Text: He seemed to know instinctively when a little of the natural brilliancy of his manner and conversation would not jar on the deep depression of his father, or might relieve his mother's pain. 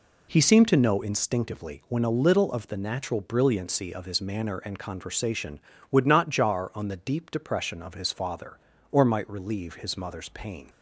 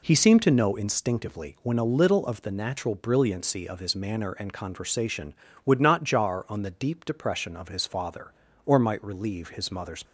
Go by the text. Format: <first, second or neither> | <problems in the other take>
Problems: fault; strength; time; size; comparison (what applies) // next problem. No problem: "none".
first | stops before "pain"; at 10.0 s